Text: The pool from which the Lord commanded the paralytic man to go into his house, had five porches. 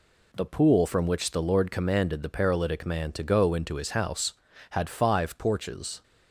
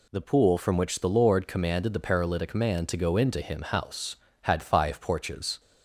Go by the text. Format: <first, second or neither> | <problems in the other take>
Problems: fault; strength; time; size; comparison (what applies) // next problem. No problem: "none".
first | says "him" for "his"; at 3.4 s